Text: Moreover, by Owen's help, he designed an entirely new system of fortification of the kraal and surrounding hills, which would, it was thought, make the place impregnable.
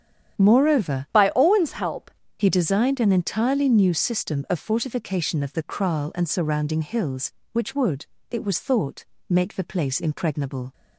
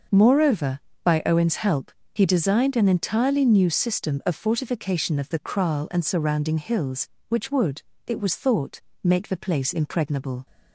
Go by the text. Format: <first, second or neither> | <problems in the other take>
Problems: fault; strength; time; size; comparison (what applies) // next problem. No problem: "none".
second | starts louder than the rest; strong; until 1.4 s; 9 dB; also in the second // changes voice from "by" to "help"; from 1.1 to 2.1 s; 1.0 s long